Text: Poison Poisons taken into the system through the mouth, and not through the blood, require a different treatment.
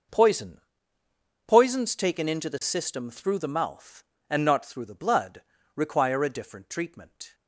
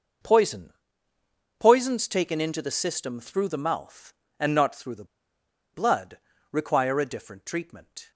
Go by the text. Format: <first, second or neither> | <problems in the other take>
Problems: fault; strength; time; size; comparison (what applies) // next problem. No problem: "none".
first | pauses between "Poison" and "Poisons"; noticeable; at 0.7 s; 0.86 s long; noticeable in the first // pauses between "the" and "blood"; noticeable; at 5.0 s; 0.69 s long